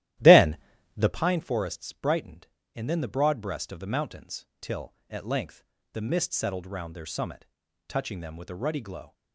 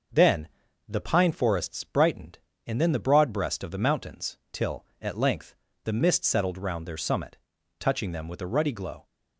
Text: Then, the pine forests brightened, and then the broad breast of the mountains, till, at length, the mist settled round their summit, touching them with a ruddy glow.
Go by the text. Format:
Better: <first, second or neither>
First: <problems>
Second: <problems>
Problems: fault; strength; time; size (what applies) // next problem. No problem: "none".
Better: second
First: starts louder than the rest; strong; until 1.2 s; 14 dB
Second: none